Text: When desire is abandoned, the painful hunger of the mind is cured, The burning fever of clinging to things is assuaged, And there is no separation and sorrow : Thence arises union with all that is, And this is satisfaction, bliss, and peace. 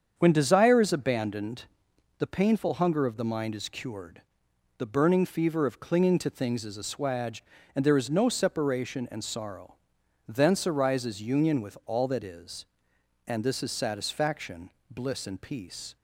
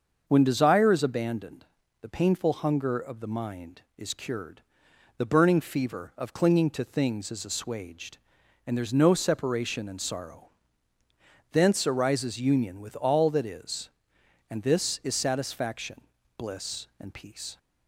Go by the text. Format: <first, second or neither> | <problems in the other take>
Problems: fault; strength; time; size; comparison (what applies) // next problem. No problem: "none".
neither | starts louder than the rest; the same in both